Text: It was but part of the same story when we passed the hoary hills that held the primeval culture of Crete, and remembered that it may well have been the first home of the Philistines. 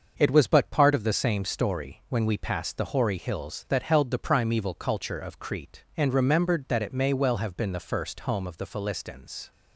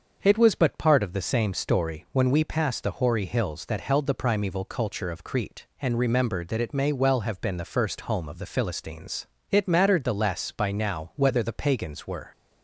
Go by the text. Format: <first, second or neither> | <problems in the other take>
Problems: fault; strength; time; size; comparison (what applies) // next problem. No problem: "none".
first | starts louder than the rest; until 1.2 s; 6.5 dB; also in the first // goes on to say "It mattered the less by now whether the pagans were"; strong; from 9.4 s on; 2.8 s long